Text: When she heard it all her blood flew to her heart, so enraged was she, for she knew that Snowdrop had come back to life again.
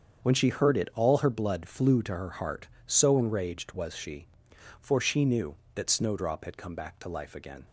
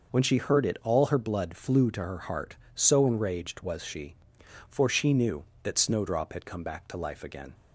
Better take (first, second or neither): second